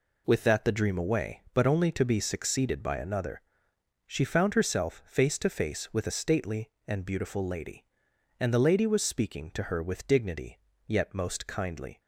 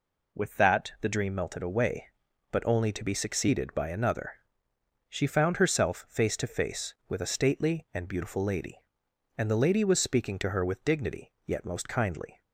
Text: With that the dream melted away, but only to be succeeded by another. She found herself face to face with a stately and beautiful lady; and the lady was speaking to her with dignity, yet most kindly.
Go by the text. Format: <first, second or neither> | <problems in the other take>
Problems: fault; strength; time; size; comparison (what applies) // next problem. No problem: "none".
second | skips "melted"; at 0.9 s